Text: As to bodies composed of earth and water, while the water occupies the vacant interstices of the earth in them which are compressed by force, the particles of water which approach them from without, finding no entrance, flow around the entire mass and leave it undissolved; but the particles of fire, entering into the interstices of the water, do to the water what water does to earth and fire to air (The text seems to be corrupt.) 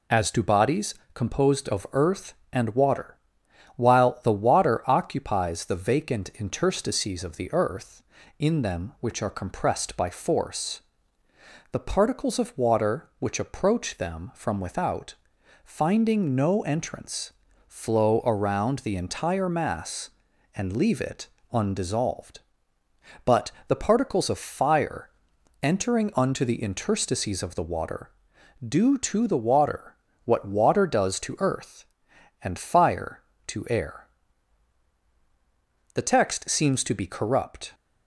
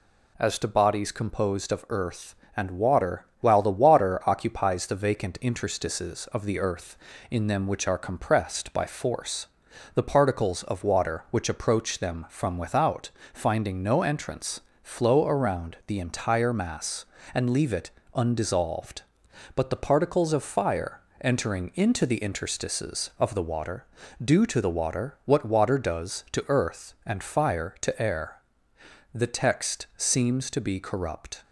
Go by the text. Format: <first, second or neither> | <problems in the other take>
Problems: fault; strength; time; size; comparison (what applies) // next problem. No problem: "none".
second | pauses between "bodies" and "composed"; slight; at 0.9 s; 0.18 s long // pauses between "it" and "undissolved"; slight; at 21.2 s; 0.24 s long; slight in the second // pauses between "but" and "the"; slight; at 23.5 s; 0.16 s long // says "unto" for "into"; at 26.1 s // pauses between "water" and "what"; slight; at 29.9 s; 0.28 s long